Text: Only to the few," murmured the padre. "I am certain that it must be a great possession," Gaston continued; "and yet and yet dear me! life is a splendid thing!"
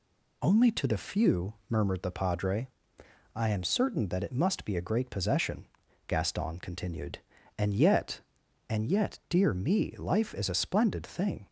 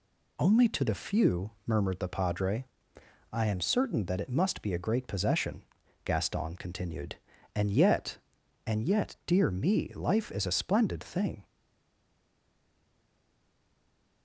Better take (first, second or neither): first